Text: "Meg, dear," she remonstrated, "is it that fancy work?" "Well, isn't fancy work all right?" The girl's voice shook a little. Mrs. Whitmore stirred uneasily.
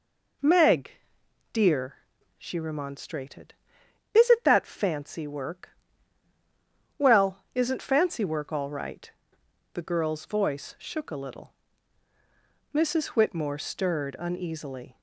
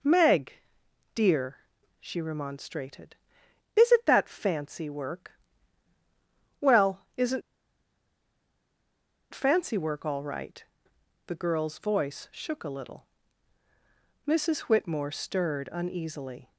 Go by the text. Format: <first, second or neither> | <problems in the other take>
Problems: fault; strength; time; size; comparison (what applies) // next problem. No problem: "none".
first | pauses between "isn't" and "fancy"; strong; at 7.4 s; 1.9 s long